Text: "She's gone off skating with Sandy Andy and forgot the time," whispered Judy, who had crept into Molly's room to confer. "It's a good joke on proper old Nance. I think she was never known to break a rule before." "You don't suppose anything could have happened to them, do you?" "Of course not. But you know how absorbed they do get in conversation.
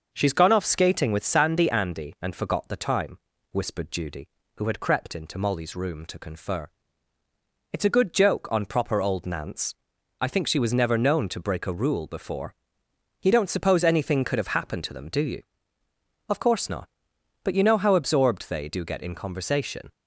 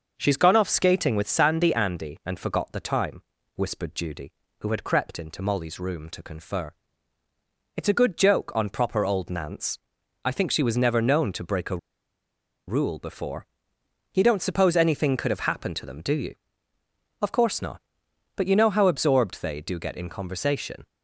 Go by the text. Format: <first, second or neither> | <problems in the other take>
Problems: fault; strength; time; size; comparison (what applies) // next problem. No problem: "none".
first | pauses between "a" and "rule"; noticeable; at 11.7 s; 0.90 s long